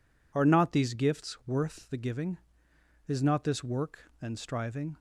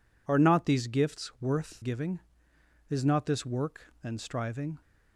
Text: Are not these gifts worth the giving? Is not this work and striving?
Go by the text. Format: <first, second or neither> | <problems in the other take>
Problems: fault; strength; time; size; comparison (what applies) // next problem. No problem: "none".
first | skips "the"; at 1.8 s